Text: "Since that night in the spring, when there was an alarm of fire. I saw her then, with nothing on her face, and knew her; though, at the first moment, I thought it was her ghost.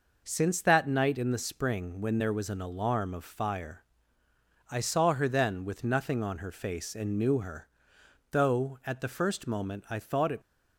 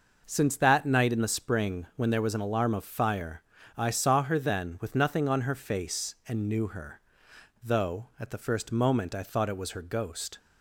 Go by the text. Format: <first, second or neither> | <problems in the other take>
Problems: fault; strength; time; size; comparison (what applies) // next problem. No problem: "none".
second | stops before "was her ghost"; at 10.4 s